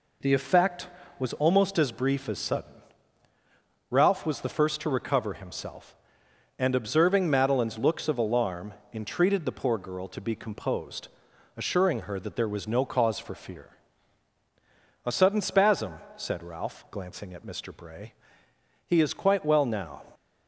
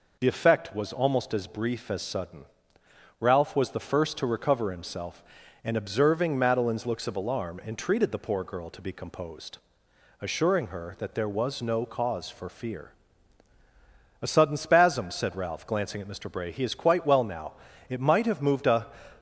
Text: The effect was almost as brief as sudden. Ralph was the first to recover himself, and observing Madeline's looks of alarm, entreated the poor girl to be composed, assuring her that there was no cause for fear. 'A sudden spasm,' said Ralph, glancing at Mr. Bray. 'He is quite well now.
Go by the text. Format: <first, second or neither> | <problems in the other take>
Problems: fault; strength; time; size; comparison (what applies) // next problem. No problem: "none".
first | goes on to say "It might have moved a"; noticeable; from 17.8 s on; 1.0 s long